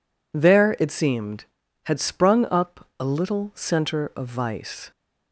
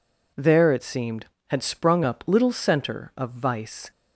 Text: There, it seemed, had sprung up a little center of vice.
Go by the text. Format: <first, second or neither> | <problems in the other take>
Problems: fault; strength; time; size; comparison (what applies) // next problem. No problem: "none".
first | skips "a"; at 2.2 s